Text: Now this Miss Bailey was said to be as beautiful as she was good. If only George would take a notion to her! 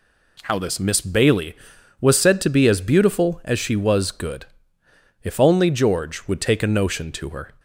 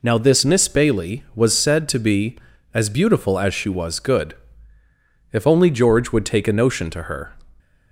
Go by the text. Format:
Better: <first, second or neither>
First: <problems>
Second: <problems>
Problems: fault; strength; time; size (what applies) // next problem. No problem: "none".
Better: second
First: says "How" for "Now"; at 0.4 s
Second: none